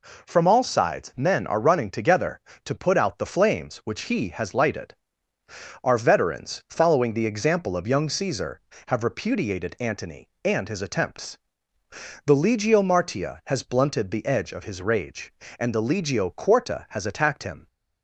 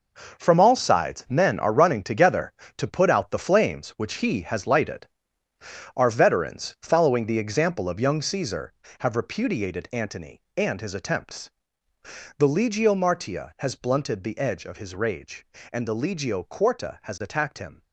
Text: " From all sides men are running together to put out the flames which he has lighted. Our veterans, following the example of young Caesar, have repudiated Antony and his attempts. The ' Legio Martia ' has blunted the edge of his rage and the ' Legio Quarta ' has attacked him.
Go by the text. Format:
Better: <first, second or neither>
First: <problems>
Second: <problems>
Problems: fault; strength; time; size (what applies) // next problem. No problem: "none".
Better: first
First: none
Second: gets quieter; strong; throughout; 11.5 dB